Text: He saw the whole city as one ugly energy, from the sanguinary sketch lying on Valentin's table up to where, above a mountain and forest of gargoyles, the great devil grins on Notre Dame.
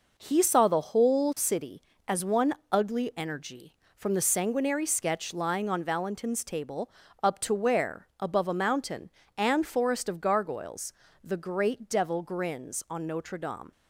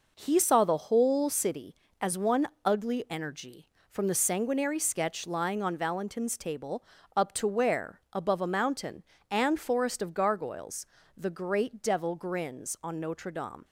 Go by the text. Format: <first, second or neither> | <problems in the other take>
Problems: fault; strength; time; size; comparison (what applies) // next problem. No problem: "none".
neither | pauses between "one" and "ugly"; slight; the same in both // pauses between "table" and "up"; slight; the same in both